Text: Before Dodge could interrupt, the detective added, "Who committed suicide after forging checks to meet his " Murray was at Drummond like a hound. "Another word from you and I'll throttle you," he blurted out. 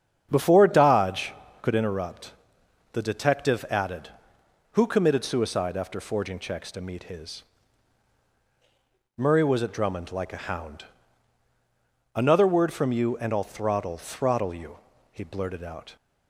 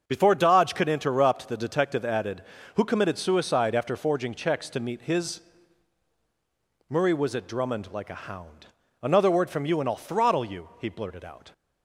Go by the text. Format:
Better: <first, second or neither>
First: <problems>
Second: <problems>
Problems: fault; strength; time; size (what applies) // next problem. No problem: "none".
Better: second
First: starts louder than the rest; strong; until 1.3 s; 10.5 dB // says "throttle" twice; at 13.9 s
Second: starts louder than the rest; strong; until 1.0 s; 7 dB